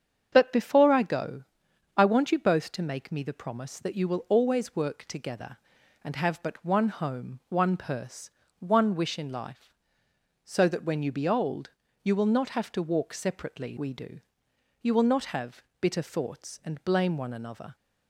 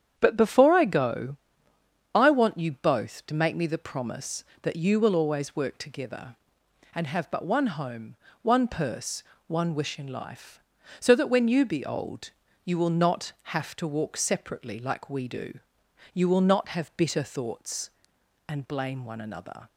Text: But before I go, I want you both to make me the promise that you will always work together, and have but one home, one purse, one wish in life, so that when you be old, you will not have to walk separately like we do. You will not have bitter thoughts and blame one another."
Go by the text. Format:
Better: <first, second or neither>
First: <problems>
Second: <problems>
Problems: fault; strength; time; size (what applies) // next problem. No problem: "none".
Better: second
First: starts louder than the rest; strong; until 1.3 s; 7.5 dB // skips "like"; at 13.7 s // pauses between "have" and "bitter"; slight; at 15.6 s; 0.16 s long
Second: starts louder than the rest; strong; until 1.1 s; 8.5 dB